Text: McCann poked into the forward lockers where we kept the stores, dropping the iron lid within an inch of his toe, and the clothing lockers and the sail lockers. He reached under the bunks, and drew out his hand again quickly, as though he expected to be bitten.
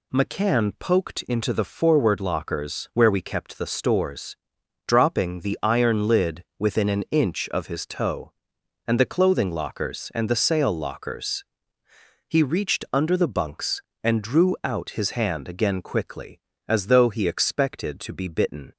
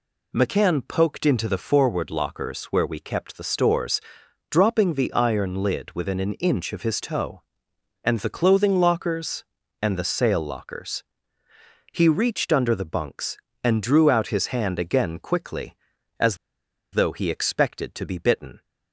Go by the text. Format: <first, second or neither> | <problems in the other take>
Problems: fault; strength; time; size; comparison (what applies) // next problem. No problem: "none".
first | pauses between "as" and "though"; noticeable; at 16.3 s; 0.56 s long